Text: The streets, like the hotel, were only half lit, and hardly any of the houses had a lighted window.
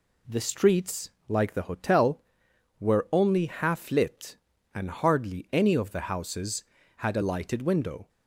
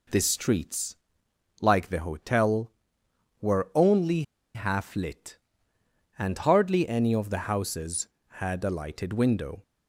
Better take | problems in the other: first | pauses between "only" and "half"; slight; at 4.2 s; 0.32 s long

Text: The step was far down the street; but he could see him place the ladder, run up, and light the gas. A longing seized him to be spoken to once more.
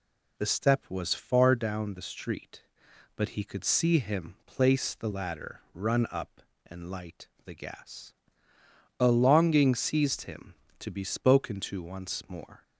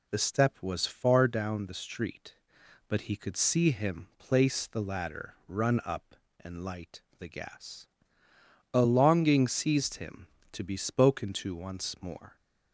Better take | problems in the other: neither | pauses between "light" and "the"; slight; the same in both

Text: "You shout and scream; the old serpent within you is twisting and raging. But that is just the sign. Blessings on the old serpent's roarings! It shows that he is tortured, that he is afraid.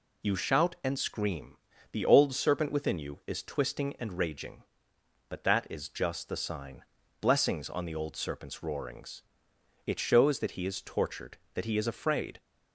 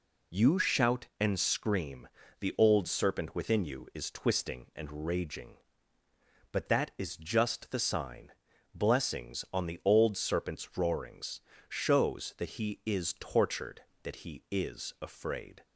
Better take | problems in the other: first | skips "It"; at 11.5 s

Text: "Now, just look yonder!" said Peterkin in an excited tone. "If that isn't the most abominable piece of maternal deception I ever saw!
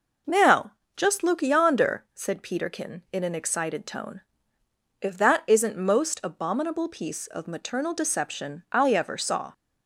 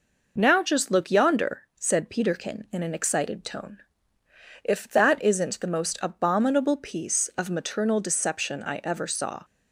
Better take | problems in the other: second | skips "the"; at 5.7 s

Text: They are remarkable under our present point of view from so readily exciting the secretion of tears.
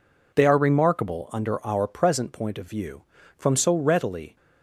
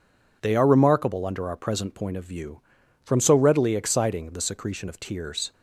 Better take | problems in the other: second | stops before "exciting the secretion of tears"; at 4.3 s

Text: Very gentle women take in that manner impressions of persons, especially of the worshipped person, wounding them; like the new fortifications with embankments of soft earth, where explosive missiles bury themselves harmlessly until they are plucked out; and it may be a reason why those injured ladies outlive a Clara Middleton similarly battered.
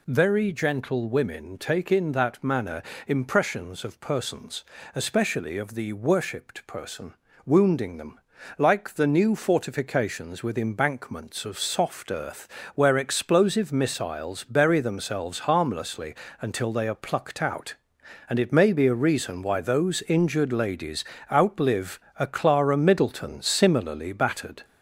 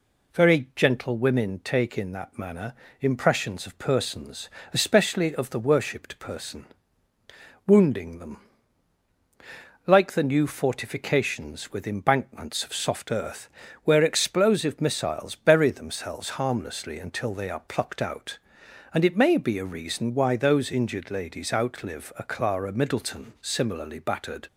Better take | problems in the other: second | gets louder; noticeable; throughout; 4 dB // pauses between "manner" and "impressions"; slight; at 2.8 s; 0.24 s long; slight in the second // pauses between "harmlessly" and "until"; slight; at 16.1 s; 0.28 s long // pauses between "ladies" and "outlive"; slight; at 21.0 s; 0.30 s long // pauses between "outlive" and "a"; slight; at 21.9 s; 0.20 s long

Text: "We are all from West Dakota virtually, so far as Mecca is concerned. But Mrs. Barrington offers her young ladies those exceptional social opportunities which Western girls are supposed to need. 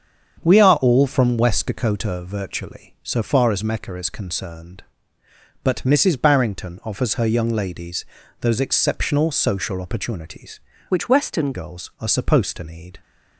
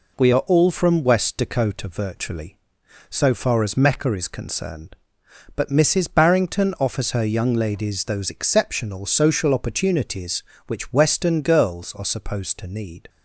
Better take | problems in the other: second | starts louder than the rest; strong; until 1.4 s; 7.5 dB // pauses between "ladies" and "those"; slight; at 8.0 s; 0.36 s long // changes voice from "which" to "Western"; from 10.8 to 11.5 s; 0.7 s long

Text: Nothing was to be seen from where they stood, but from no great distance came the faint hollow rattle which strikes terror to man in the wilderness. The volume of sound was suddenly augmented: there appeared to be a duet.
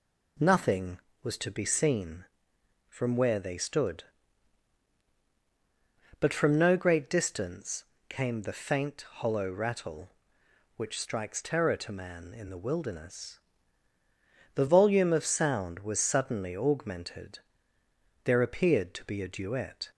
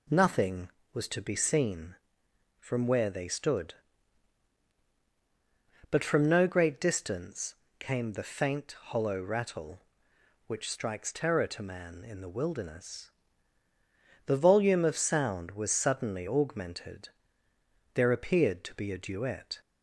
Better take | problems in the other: neither | pauses between "distance" and "came"; slight; the same in both

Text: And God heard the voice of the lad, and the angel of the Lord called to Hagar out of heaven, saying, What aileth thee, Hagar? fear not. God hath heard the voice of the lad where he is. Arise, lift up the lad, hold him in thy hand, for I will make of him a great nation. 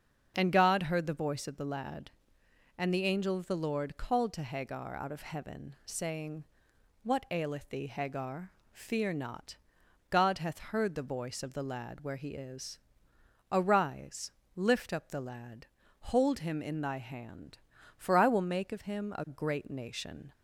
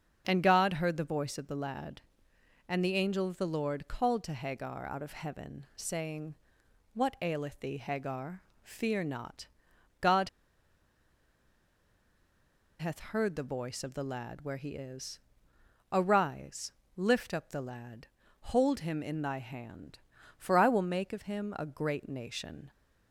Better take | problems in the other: first | starts louder than the rest; until 1.2 s; 6.5 dB; also in the first // pauses between "God" and "hath"; strong; at 10.2 s; 2.5 s long

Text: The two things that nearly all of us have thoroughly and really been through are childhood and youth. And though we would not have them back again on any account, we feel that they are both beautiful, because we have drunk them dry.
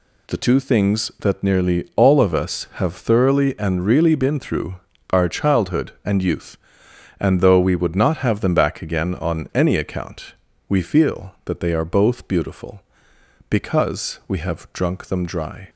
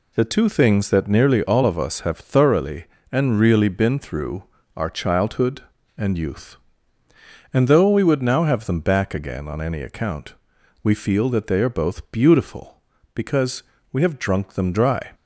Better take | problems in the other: first | says "now" for "not"; at 8.2 s // pauses between "because" and "we"; slight; at 13.6 s; 0.30 s long

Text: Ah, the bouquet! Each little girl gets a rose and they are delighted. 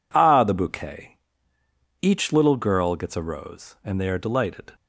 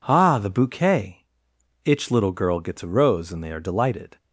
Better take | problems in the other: first | says "Itch" for "Each"; at 1.8 s

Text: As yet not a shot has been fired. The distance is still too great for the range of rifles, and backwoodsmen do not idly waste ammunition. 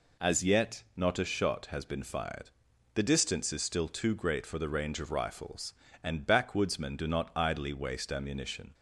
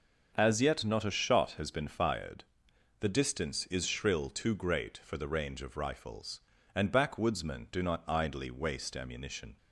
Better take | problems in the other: first | starts louder than the rest; until 1.3 s; 6.5 dB // says "shrill" for "still"; at 3.8 s

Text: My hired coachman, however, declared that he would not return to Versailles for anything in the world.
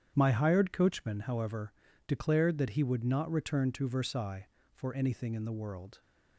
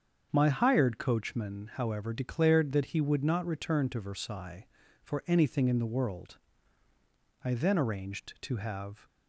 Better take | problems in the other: first | starts louder than the rest; strong; until 1.3 s; 7.5 dB; strong in the first // goes on to say "I then arranged to have"; from 7.4 s on; 1.6 s long

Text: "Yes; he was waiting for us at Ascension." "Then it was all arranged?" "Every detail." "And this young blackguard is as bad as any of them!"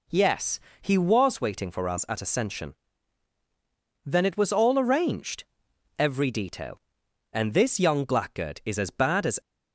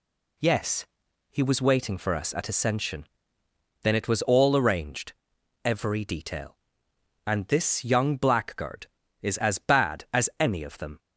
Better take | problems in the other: second | stops before "any of them"; at 9.4 s

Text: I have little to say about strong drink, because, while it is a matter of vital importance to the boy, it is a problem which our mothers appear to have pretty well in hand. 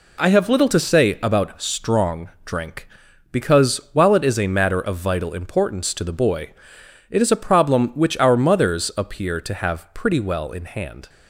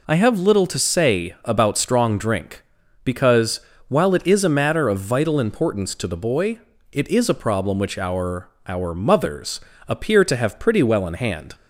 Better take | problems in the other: first | says "our" twice; at 8.6 s // pauses between "mothers" and "appear"; slight; at 9.5 s; 0.28 s long

